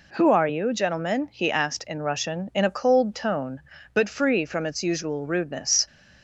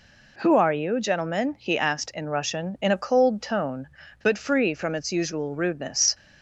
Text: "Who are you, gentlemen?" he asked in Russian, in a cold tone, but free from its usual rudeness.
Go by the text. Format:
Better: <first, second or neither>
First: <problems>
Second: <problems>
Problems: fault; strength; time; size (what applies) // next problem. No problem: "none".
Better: neither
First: none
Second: none